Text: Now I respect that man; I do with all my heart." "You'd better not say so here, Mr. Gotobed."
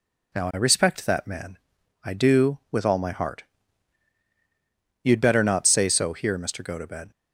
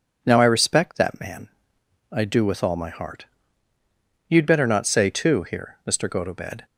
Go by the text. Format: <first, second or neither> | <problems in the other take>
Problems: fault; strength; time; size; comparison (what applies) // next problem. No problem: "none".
first | says "too" for "so"; at 5.0 s